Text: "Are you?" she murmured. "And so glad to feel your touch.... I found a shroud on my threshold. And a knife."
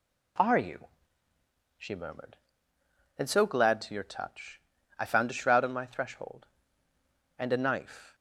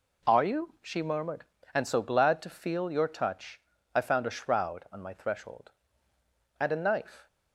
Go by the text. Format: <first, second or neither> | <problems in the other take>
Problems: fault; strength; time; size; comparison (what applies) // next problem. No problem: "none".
second | skips "feel"; at 3.9 s